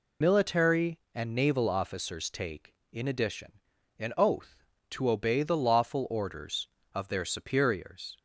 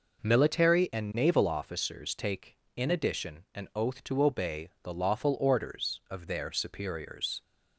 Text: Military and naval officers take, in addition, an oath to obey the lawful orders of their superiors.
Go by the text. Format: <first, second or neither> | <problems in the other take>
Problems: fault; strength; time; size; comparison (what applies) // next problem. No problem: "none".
second | loses the start of "Military"; at 0.2 s; 50 ms